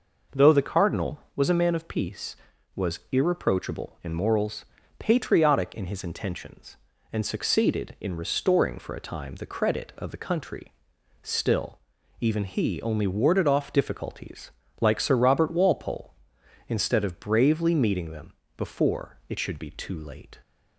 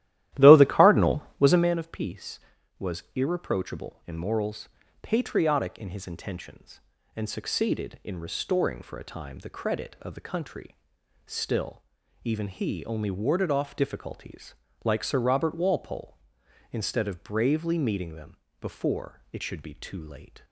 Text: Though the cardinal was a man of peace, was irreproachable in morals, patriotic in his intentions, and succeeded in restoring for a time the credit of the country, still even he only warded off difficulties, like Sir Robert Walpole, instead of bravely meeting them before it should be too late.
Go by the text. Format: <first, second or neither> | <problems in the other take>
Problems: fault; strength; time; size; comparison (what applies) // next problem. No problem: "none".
first | starts louder than the rest; strong; until 1.8 s; 13.5 dB // pauses between "still" and "even"; at 11.8 s; 0.42 s long; also in the first // pauses between "them" and "before"; slight; at 18.3 s; 0.24 s long; slight in the first